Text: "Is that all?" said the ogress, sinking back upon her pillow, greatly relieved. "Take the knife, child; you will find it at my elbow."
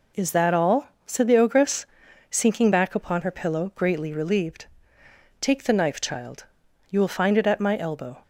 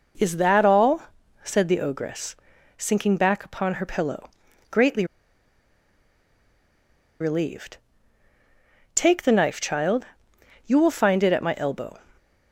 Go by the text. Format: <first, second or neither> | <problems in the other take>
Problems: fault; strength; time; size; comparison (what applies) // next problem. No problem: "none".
first | pauses between "greatly" and "relieved"; strong; at 5.0 s; 2.1 s long